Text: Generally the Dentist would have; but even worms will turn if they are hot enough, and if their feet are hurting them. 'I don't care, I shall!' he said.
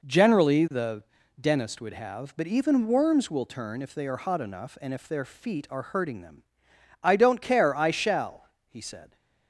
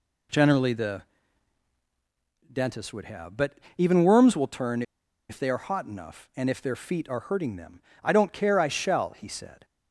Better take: first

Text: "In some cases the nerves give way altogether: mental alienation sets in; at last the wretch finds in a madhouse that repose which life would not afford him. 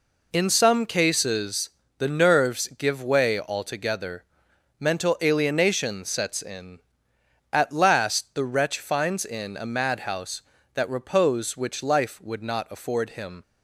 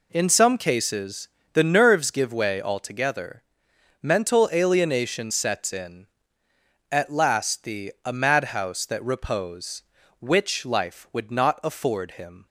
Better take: first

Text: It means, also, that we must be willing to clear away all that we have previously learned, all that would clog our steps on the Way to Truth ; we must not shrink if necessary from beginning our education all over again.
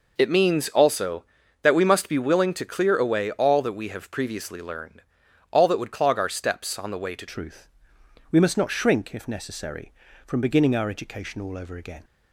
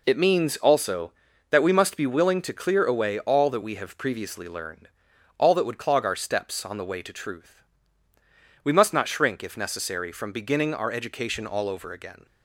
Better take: second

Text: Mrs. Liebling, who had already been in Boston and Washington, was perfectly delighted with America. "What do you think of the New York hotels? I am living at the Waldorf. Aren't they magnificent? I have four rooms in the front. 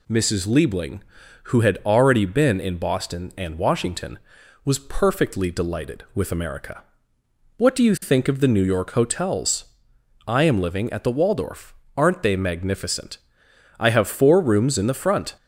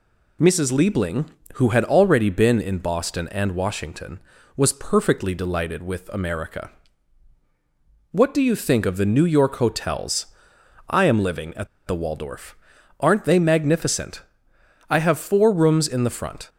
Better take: first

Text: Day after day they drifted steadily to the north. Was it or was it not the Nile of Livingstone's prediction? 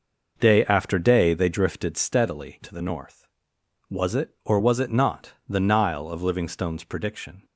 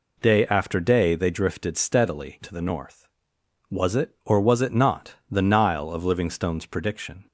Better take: second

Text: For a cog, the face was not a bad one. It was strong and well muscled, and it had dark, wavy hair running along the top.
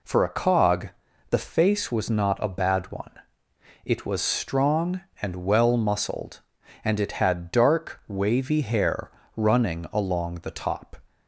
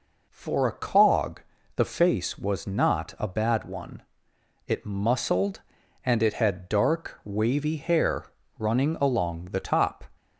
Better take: first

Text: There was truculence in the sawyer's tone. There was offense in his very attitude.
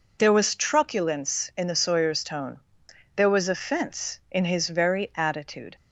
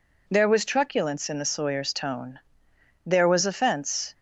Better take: first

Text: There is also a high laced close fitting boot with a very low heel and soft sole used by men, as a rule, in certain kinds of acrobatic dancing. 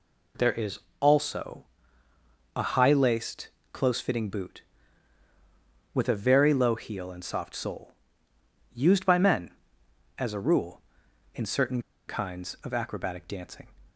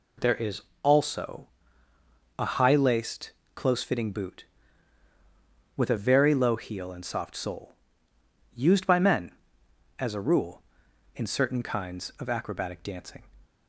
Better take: second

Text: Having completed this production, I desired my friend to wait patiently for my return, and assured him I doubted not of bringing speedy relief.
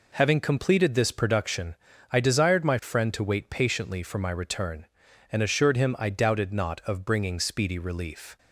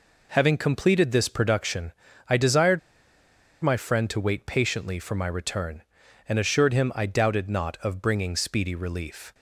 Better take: first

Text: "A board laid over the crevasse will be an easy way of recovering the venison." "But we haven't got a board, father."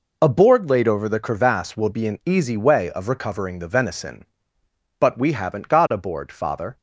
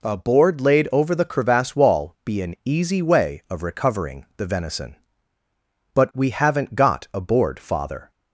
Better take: first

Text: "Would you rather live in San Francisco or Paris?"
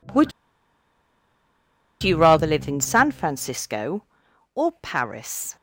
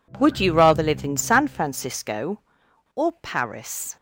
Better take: second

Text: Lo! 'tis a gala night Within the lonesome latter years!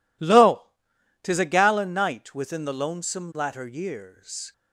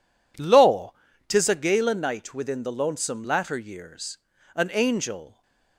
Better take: first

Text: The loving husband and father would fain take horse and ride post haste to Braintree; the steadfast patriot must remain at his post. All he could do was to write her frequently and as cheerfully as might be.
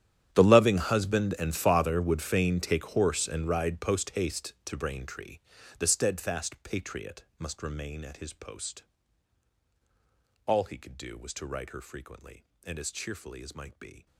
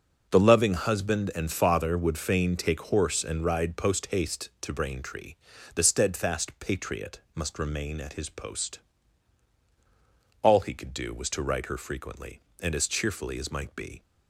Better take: second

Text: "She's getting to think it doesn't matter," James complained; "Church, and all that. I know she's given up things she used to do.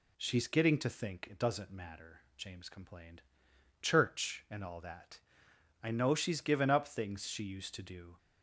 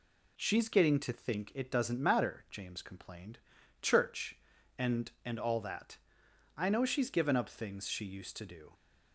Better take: first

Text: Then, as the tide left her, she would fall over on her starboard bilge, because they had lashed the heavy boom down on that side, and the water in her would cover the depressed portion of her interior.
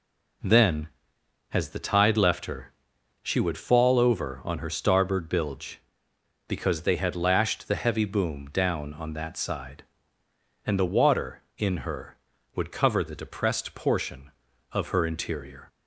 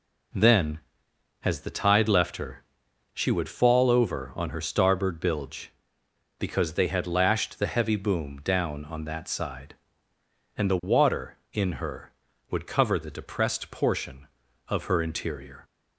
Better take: neither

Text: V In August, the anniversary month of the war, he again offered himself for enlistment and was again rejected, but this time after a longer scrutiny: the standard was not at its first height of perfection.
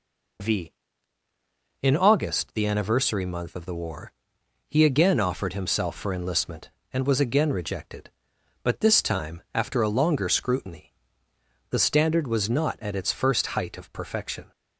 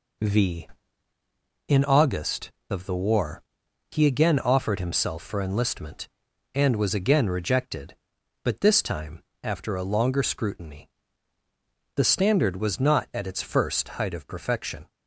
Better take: first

